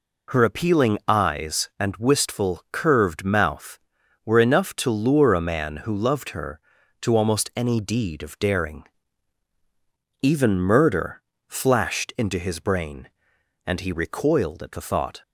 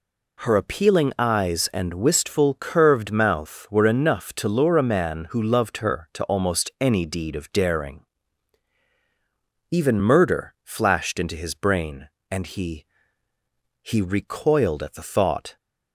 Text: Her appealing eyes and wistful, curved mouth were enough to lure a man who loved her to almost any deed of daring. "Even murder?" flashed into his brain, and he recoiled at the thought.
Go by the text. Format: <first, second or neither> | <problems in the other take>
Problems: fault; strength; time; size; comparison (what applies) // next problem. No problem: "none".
first | says "he" twice; at 13.8 s